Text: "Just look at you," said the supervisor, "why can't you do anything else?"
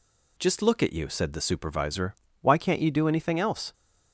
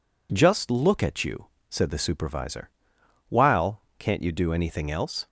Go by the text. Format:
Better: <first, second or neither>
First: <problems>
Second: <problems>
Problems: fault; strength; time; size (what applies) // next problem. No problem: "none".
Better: first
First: none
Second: says "while" for "why"; at 3.2 s